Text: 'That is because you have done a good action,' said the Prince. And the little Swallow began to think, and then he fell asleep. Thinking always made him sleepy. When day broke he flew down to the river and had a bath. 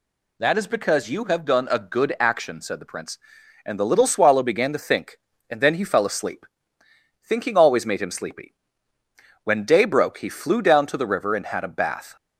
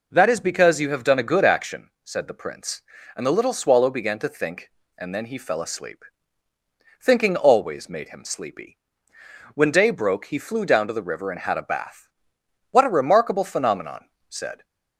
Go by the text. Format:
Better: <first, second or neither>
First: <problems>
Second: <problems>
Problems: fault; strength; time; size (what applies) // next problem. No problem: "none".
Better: first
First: none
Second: goes on to say "What a remarkable phenomenon said"; strong; from 12.7 s on; 1.9 s long